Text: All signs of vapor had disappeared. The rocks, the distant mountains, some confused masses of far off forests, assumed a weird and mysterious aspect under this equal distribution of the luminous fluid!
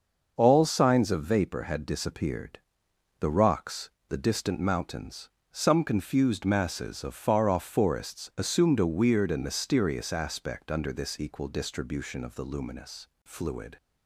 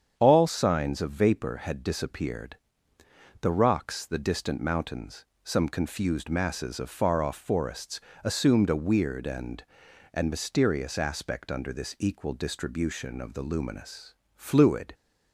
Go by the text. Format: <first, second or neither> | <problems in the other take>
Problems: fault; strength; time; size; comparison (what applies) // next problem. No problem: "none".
first | starts louder than the rest; strong; until 1.1 s; 8 dB; also in the first // says "and" twice; at 10.1 s // pauses between "luminous" and "fluid"; slight; at 14.1 s; 0.22 s long; slight in the first